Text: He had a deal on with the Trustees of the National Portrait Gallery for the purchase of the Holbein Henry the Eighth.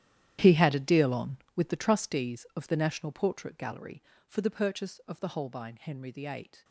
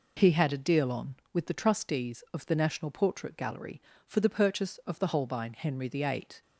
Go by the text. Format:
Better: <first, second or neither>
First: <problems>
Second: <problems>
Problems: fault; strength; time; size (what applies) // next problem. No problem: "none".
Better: second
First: gets quieter; strong; throughout; 15.5 dB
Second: none